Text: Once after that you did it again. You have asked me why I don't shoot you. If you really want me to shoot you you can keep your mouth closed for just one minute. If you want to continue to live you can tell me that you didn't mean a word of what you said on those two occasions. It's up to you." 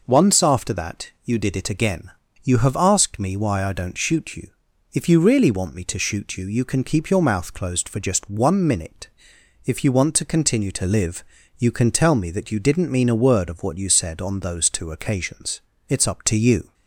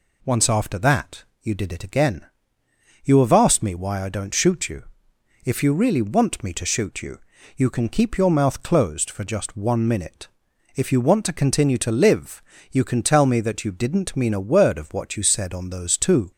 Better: first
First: pauses between "live" and "you"; slight; at 11.2 s; 0.34 s long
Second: pauses between "that" and "you"; slight; at 1.2 s; 0.18 s long // pauses between "you" and "you"; at 7.1 s; 0.38 s long // pauses between "live" and "you"; slight; at 12.4 s; 0.30 s long // stops before "occasions It's up to you"; at 16.3 s

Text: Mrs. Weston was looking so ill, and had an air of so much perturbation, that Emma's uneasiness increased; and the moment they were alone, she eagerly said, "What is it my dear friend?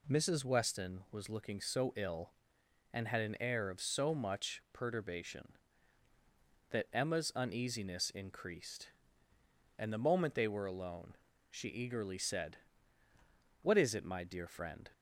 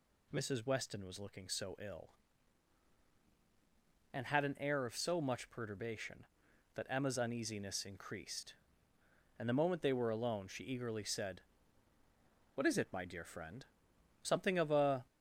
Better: first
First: none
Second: goes on to say "Something of a"; noticeable; from 14.2 s on; 0.84 s long

